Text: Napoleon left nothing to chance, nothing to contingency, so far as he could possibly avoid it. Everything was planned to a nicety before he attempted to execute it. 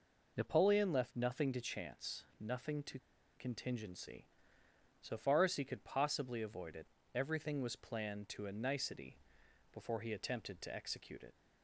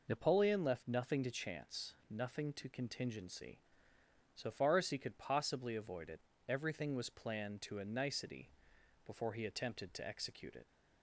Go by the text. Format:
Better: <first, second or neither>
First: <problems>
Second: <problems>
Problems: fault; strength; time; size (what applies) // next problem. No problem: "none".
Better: second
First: pauses between "to" and "contingency"; at 2.9 s; 0.39 s long // pauses between "nicety" and "before"; noticeable; at 9.1 s; 0.56 s long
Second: pauses between "nicety" and "before"; noticeable; at 8.4 s; 0.56 s long